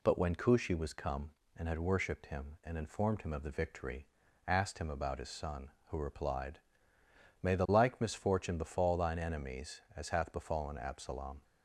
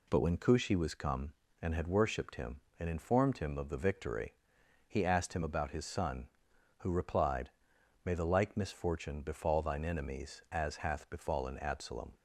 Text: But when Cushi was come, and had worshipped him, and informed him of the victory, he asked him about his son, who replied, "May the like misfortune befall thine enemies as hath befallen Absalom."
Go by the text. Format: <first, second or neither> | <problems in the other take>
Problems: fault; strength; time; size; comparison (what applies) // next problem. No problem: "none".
second | skips "he"; at 4.2 s